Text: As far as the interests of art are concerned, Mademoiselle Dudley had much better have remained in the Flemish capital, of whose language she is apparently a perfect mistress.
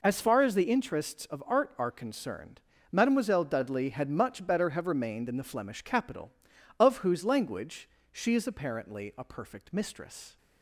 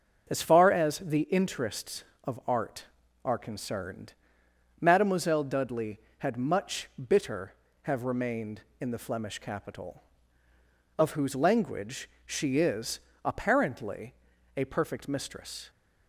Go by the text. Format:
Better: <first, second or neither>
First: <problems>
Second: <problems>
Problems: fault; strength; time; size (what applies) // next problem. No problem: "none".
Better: first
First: pauses between "language" and "she"; slight; at 7.8 s; 0.24 s long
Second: starts louder than the rest; until 1.3 s; 6 dB // says "bitter" for "better"; at 7.0 s // pauses between "language" and "she"; slight; at 12.0 s; 0.16 s long // pauses between "is" and "apparently"; slight; at 12.9 s; 0.24 s long // pauses between "apparently" and "a"; at 14.1 s; 0.42 s long